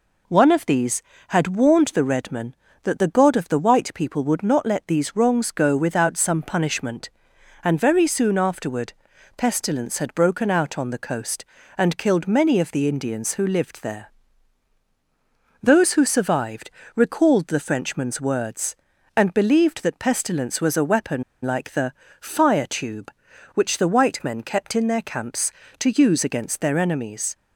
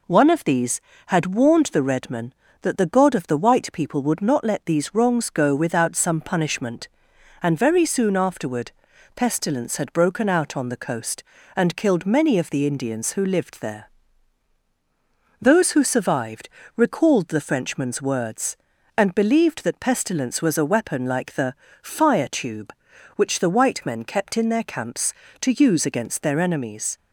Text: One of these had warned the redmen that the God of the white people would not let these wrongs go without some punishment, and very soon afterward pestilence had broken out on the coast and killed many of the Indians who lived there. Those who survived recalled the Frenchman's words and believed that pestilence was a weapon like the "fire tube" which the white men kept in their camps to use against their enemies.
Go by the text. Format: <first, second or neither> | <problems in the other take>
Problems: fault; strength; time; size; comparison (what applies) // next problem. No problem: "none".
second | pauses between "afterward" and "pestilence"; at 8.9 s; 0.44 s long; also in the second // pauses between "survived" and "recalled"; slight; at 16.7 s; 0.24 s long; slight in the second // pauses between "weapon" and "like"; slight; at 21.2 s; 0.21 s long // pauses between "the" and "fire"; slight; at 21.9 s; 0.28 s long; slight in the second